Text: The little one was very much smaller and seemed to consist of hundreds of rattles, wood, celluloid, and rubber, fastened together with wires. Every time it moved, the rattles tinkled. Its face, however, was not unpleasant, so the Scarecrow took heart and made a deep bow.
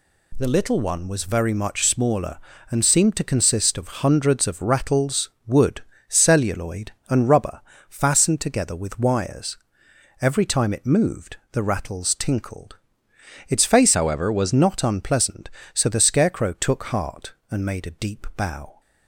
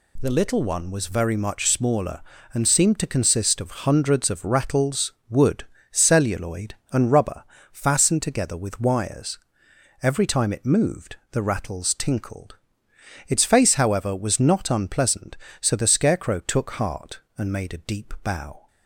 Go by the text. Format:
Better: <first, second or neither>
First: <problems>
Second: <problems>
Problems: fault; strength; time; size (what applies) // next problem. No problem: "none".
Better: second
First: changes voice from "however" to "was"; from 13.9 to 14.5 s; 0.6 s long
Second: none